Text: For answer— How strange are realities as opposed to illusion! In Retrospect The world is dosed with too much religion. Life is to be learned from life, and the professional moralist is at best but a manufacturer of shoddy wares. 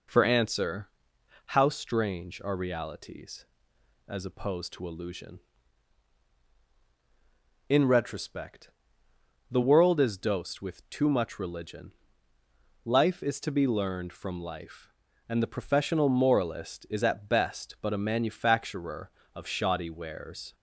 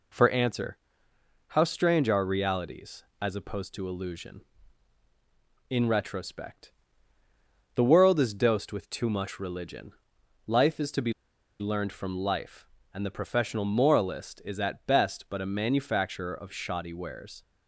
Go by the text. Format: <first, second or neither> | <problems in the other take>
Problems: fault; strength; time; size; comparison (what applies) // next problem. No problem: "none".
first | pauses between "Retrospect" and "The"; at 6.7 s; 1.0 s long; noticeable in the first // pauses between "be" and "learned"; noticeable; at 11.1 s; 0.48 s long